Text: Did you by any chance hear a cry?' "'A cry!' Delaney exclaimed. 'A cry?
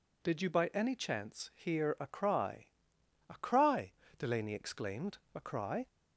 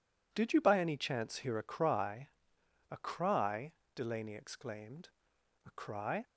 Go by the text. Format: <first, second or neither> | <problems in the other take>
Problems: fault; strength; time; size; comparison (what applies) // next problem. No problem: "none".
neither | none